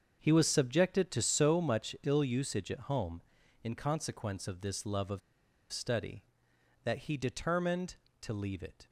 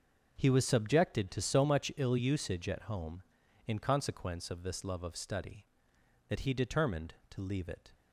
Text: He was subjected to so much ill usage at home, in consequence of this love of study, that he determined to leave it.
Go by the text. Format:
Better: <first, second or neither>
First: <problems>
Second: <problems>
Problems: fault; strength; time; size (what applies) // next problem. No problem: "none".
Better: second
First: starts louder than the rest; until 1.2 s; 7 dB // pauses between "of" and "study"; noticeable; at 5.2 s; 0.52 s long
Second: starts louder than the rest; noticeable; until 1.3 s; 6 dB